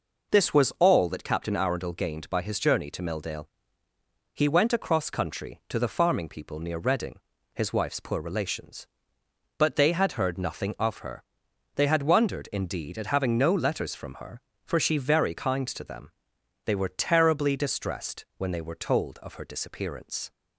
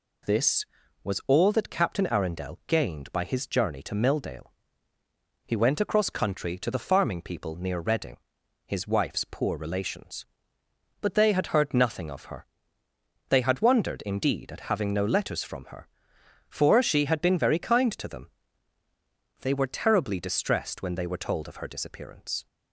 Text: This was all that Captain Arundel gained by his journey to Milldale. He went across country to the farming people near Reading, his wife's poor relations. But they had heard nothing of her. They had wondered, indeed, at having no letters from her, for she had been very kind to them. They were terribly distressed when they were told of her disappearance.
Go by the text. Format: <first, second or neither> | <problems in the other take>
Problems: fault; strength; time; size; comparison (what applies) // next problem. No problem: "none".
second | skips "had been"; at 14.9 s